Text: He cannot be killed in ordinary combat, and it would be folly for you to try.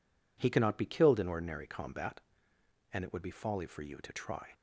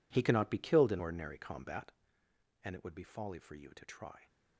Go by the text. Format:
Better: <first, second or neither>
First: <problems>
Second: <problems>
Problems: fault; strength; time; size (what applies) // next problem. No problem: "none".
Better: first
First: none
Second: gets quieter; strong; throughout; 16 dB